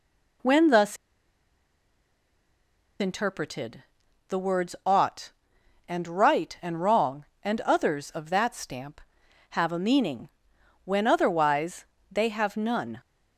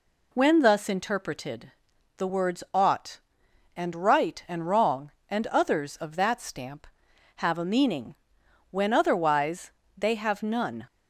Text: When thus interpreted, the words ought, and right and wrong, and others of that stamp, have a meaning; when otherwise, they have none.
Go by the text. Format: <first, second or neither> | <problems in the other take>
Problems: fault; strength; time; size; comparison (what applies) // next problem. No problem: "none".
second | pauses between "thus" and "interpreted"; strong; at 0.9 s; 2.0 s long